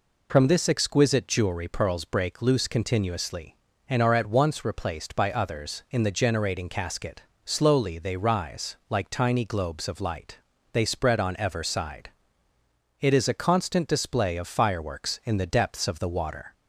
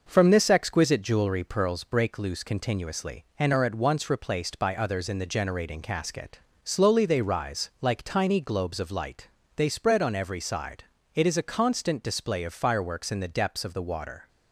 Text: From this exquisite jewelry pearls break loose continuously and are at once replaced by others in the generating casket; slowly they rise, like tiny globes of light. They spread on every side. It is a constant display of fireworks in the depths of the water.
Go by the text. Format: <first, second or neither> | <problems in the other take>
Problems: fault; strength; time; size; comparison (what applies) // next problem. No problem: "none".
second | says "ever" for "every"; at 11.3 s